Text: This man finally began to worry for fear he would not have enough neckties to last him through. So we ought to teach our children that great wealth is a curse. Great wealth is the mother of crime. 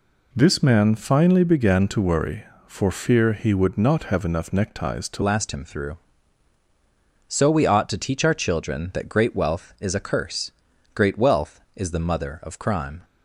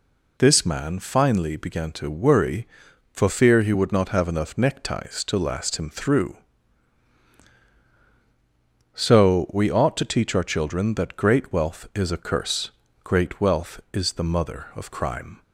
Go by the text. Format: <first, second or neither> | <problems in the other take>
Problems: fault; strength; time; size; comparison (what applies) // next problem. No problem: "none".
second | changes voice at "last"; from 5.2 s on; 7.8 s long